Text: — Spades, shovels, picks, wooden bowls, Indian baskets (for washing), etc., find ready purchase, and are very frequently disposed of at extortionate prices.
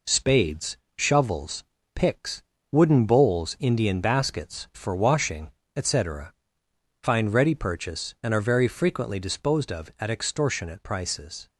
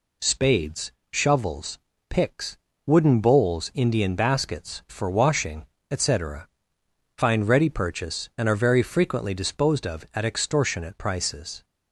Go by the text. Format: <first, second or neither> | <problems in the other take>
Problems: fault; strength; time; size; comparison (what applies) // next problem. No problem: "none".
second | gets quieter; noticeable; throughout; 5 dB